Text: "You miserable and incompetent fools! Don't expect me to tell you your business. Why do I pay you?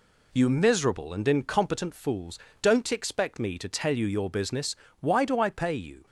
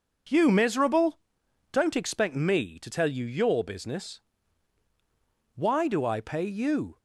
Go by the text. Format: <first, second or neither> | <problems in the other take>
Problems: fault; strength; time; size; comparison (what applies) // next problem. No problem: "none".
first | skips "and incompetent fools"; at 1.4 s